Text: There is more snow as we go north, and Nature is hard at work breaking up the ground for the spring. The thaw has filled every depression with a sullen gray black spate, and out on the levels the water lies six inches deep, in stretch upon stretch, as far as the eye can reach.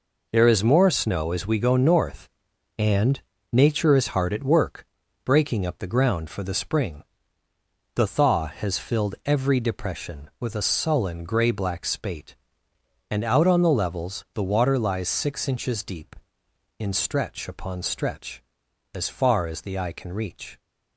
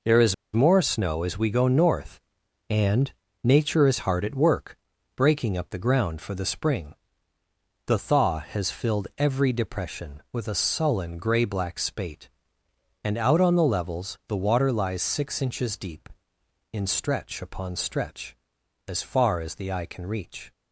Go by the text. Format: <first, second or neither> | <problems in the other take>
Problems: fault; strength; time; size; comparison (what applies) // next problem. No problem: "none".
first | pauses between "is" and "more"; slight; at 0.3 s; 0.18 s long // pauses between "and" and "Nature"; slight; at 3.0 s; 0.32 s long; slight in the first // pauses between "work" and "breaking"; at 4.7 s; 0.40 s long; also in the first